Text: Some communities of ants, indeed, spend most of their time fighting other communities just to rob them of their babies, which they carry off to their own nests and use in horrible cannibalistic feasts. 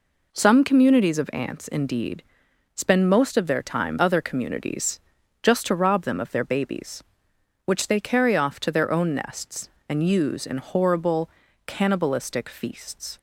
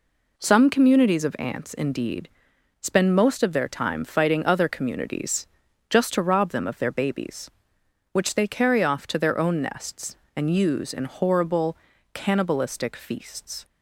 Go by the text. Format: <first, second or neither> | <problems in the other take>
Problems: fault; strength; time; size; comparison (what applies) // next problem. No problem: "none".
second | skips "fighting"; at 3.9 s // pauses between "communities" and "just"; at 4.9 s; 0.42 s long; also in the second // pauses between "horrible" and "cannibalistic"; slight; at 11.2 s; 0.36 s long; slight in the second